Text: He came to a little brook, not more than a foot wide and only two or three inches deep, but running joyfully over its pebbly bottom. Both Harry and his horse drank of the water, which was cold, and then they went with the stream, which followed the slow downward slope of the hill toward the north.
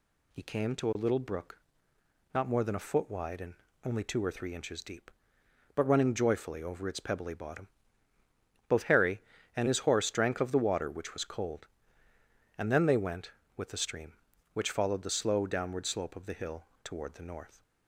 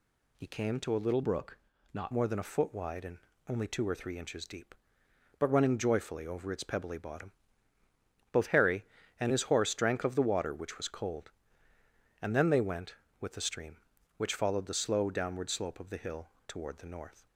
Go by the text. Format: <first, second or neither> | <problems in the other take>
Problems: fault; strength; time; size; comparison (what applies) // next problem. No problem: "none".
first | changes voice from "brook" to "not"; from 1.2 to 2.1 s; 0.9 s long // pauses between "and" and "only"; slight; at 3.1 s; 0.30 s long; slight in the first // pauses between "hill" and "toward"; slight; at 16.2 s; 0.18 s long; slight in the first